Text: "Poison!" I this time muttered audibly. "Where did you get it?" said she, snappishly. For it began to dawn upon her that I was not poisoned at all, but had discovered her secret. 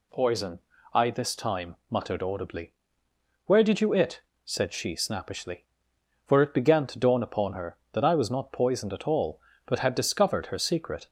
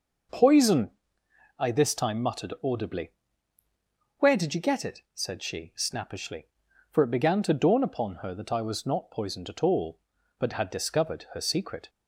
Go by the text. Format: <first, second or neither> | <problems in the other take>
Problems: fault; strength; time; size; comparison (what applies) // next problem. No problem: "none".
second | pauses between "time" and "muttered"; slight; at 1.7 s; 0.16 s long // skips "get"; at 3.9 s